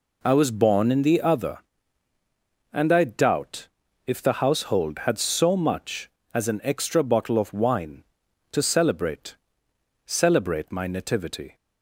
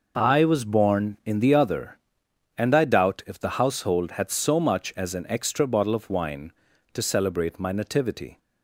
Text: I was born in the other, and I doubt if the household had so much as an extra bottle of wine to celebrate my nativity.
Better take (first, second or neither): second